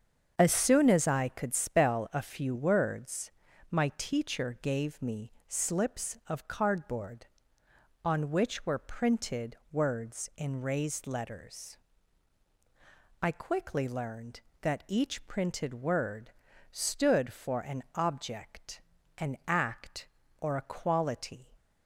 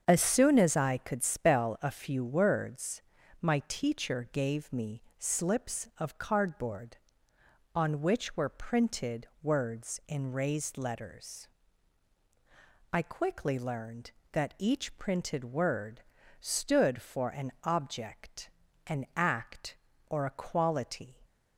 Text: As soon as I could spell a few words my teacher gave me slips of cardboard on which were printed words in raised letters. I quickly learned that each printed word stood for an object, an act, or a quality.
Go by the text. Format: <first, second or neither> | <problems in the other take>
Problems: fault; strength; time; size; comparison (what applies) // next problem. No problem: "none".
neither | starts louder than the rest; the same in both // pauses between "words" and "my"; the same in both // pauses between "me" and "slips"; slight; the same in both // pauses between "word" and "stood"; the same in both